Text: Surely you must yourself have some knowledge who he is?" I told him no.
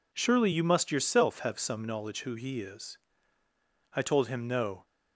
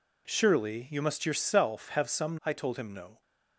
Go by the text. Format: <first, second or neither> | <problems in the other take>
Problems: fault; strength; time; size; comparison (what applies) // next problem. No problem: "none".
first | skips "knowledge who he is"; at 2.4 s